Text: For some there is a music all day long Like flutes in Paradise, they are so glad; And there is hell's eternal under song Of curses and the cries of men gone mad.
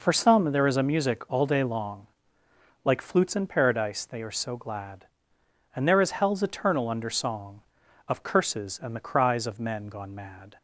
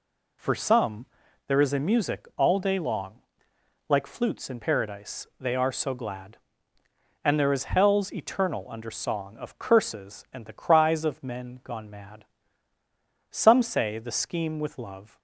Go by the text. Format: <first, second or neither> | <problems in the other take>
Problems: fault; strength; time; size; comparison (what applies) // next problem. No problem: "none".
first | pauses between "some" and "there"; at 1.0 s; 0.44 s long // pauses between "long" and "Like"; noticeable; at 3.1 s; 0.70 s long; noticeable in the first // goes on to say "Some say the Scheme with love"; strong; from 13.3 s on; 1.8 s long